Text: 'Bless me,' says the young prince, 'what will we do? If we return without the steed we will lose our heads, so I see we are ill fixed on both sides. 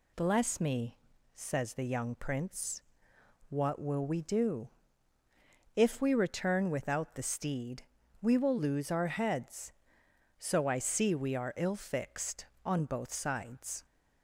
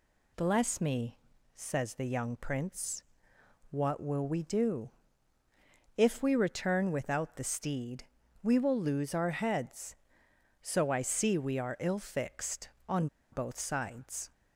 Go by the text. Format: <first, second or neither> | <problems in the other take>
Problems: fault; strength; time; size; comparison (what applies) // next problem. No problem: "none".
first | pauses between "steed" and "we"; at 8.0 s; 0.40 s long; also in the first // pauses between "on" and "both"; slight; at 13.0 s; 0.25 s long